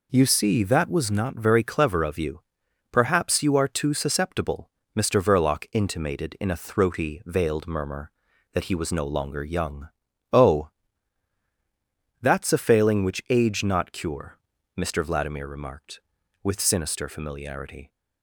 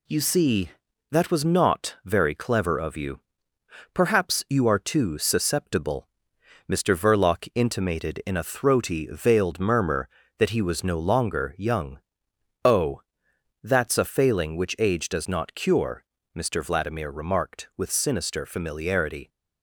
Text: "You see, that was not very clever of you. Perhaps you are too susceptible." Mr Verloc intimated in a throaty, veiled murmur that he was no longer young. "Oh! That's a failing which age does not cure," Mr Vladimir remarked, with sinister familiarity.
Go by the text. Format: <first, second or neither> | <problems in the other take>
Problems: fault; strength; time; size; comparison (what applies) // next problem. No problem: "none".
second | skips "does"; at 13.6 s